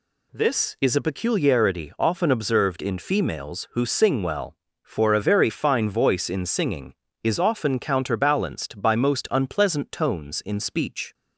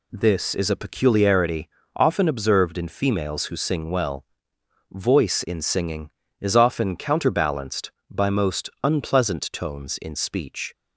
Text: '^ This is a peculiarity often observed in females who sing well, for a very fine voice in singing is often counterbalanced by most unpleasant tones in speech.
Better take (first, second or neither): first